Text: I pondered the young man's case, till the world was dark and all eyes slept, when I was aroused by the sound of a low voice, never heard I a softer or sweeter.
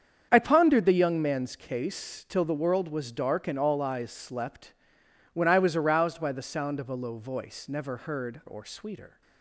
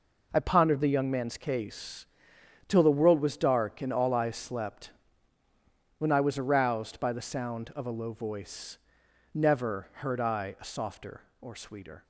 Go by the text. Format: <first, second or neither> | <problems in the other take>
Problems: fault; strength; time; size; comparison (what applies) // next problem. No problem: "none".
second | starts louder than the rest; strong; until 1.3 s; 7.5 dB // skips "I a softer"; at 8.4 s